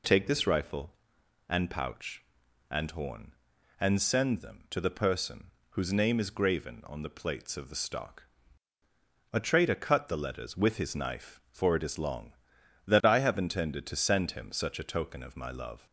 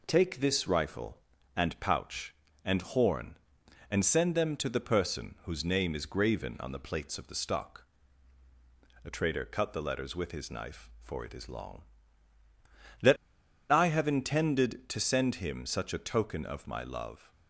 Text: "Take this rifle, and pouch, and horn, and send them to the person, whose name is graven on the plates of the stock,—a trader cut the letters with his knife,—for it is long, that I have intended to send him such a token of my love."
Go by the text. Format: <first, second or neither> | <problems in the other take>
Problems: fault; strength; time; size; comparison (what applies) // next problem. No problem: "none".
first | pauses between "that" and "I"; noticeable; at 13.1 s; 0.54 s long